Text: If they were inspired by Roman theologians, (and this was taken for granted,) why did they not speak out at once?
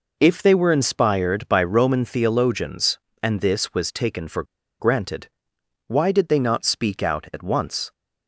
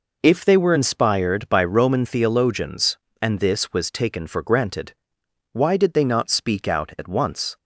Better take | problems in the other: second | pauses between "for" and "granted"; at 4.4 s; 0.36 s long

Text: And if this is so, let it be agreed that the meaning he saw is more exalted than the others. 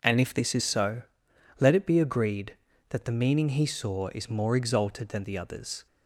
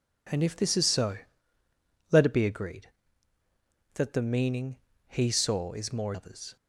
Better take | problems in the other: first | pauses between "meaning" and "he"; slight; at 4.7 s; 0.32 s long // skips "exalted than the"; at 6.1 s

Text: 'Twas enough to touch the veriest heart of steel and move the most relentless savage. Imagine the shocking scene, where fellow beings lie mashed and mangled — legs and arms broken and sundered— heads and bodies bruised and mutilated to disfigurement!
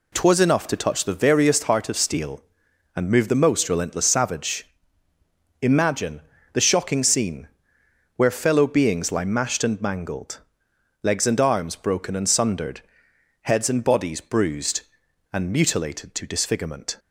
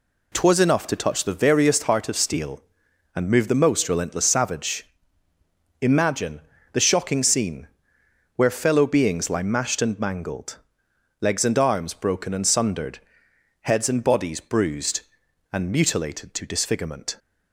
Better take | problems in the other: neither | pauses between "Imagine" and "the"; slight; the same in both

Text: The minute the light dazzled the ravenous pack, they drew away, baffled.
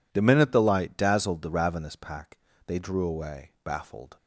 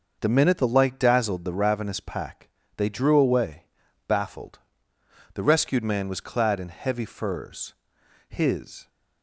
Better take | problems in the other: first | starts louder than the rest; noticeable; until 1.2 s; 6 dB // goes on to say "The rescued man was clad in heavy furs His"; strong; from 5.3 s on; 3.5 s long

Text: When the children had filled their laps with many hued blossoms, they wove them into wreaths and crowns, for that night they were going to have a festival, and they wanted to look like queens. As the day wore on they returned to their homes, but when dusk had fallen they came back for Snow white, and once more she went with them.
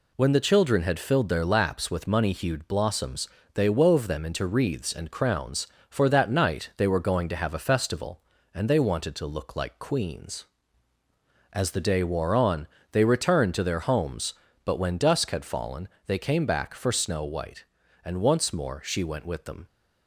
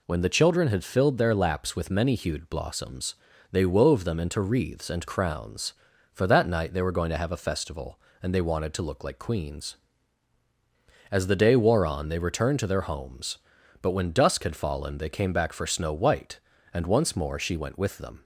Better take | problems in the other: second | says "money" for "many"; at 2.0 s // pauses between "on" and "they"; slight; at 12.6 s; 0.24 s long // pauses between "fallen" and "they"; slight; at 15.8 s; 0.18 s long

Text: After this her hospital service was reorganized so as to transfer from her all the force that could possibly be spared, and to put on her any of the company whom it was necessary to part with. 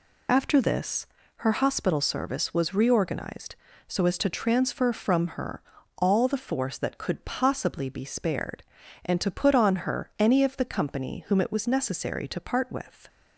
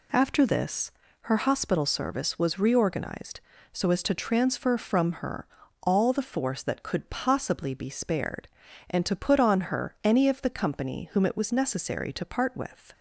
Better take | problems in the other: second | loses the start of "After"; at 0.2 s; 45 ms // pauses between "this" and "her"; slight; at 1.0 s; 0.34 s long; slight in the second // pauses between "her" and "all"; slight; at 5.6 s; 0.36 s long; slight in the second

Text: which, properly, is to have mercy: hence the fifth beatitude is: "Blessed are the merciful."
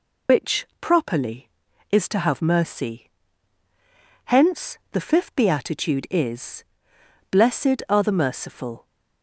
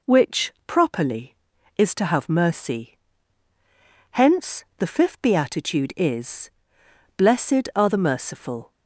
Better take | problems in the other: second | loses the start of "which"; at 0.2 s; 115 ms

